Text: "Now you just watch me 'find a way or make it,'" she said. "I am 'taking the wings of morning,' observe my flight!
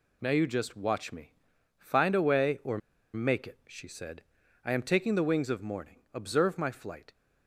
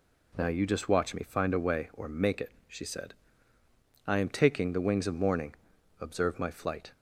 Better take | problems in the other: second | pauses between "me" and "find"; noticeable; at 1.3 s; 0.46 s long // pauses between "or" and "make"; at 2.7 s; 0.36 s long

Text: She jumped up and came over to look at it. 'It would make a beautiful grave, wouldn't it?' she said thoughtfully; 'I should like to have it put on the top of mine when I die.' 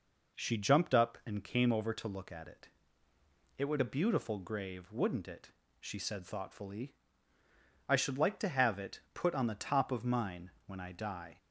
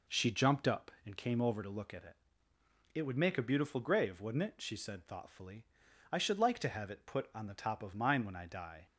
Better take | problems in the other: second | skips "make"; at 3.7 s

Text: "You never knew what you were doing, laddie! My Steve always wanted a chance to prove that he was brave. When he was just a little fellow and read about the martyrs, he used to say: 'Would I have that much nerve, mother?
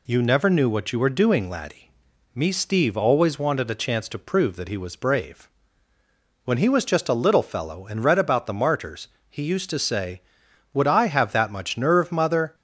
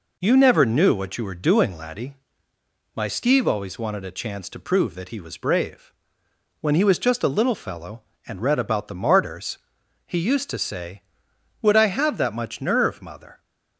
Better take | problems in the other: second | says "Me" for "My"; at 2.3 s

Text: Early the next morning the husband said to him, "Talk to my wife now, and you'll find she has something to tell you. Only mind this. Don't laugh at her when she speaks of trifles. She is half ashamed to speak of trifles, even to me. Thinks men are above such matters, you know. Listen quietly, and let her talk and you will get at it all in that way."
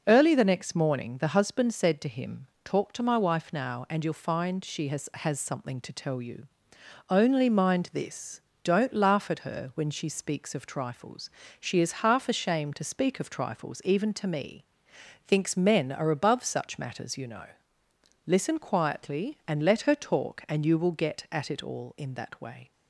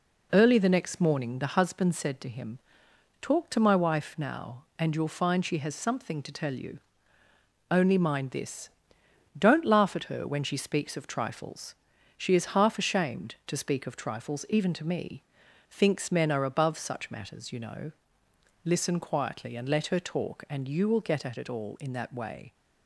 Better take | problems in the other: second | says "has" twice; at 5.1 s

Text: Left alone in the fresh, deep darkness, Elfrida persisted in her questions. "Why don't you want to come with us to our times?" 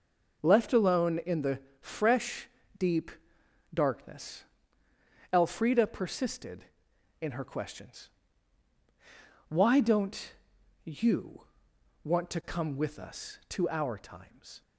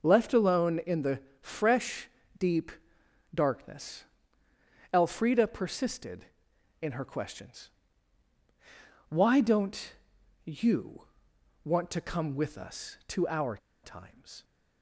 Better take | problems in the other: first | starts louder than the rest; until 1.0 s; 6.5 dB; also in the first // pauses between "the" and "fresh"; slight; at 1.2 s; 0.22 s long; slight in the first // pauses between "deep" and "darkness"; noticeable; at 2.7 s; 0.62 s long; noticeable in the first // pauses between "don't" and "you"; noticeable; at 9.9 s; 0.52 s long; noticeable in the first // pauses between "you" and "want"; noticeable; at 11.0 s; 0.58 s long; noticeable in the first // pauses between "our" and "times"; slight; at 13.5 s; 0.25 s long

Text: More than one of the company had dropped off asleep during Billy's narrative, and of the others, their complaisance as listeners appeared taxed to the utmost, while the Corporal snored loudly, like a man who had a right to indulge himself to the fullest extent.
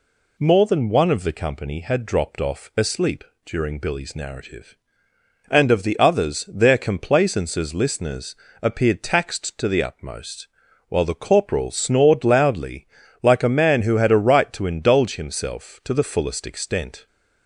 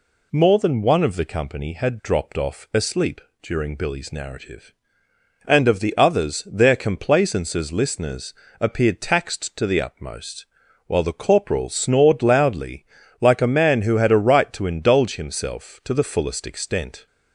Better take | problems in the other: neither | pauses between "asleep" and "during"; slight; the same in both // pauses between "listeners" and "appeared"; slight; the same in both

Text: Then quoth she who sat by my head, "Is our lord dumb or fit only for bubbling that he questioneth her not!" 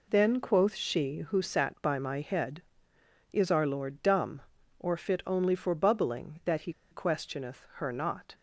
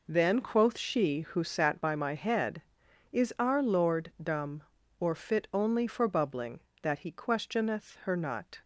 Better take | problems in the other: second | pauses between "he" and "questioneth"; slight; at 6.7 s; 0.19 s long

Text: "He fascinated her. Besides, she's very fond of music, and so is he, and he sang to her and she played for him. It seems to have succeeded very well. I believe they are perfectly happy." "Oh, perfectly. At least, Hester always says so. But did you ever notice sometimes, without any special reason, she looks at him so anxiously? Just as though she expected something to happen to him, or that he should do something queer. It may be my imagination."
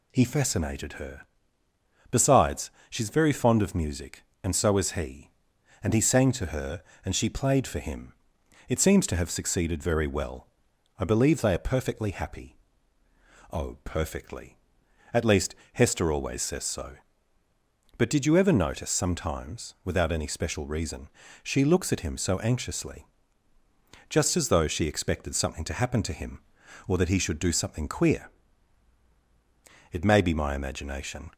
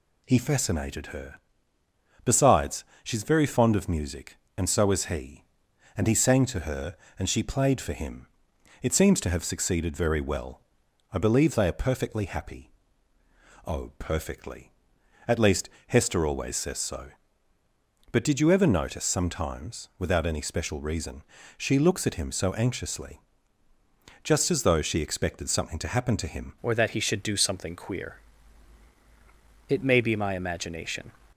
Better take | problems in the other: first | changes voice at "or"; from 26.6 s on; 4.5 s long

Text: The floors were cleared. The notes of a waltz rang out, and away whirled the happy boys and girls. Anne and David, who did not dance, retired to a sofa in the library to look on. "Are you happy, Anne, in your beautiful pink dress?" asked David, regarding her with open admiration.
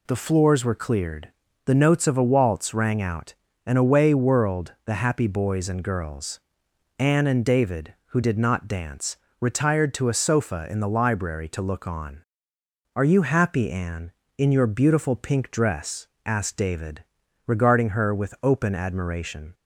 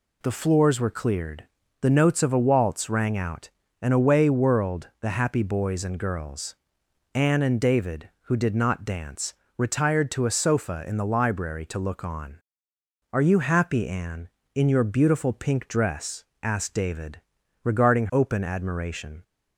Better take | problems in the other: first | skips "her with"; at 18.0 s

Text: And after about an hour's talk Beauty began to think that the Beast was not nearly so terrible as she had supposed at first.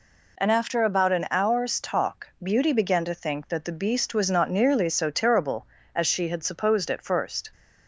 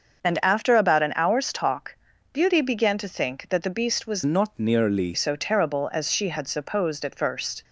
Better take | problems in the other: first | starts louder than the rest; until 1.2 s; 6.5 dB // pauses between "talk" and "Beauty"; at 1.9 s; 0.38 s long; slight in the first // changes voice from "not" to "nearly"; from 4.2 to 5.1 s; 0.9 s long

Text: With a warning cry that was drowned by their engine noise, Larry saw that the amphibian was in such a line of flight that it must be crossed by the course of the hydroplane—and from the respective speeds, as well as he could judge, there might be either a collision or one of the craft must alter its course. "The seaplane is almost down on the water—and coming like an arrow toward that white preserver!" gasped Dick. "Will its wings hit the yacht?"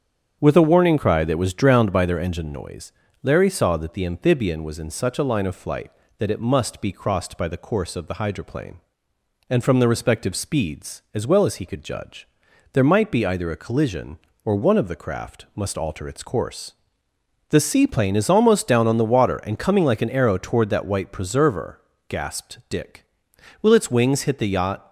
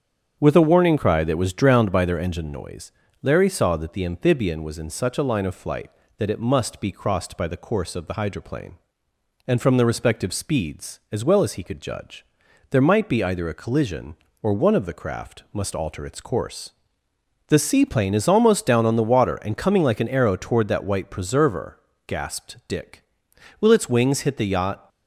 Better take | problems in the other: neither | starts louder than the rest; strong; the same in both

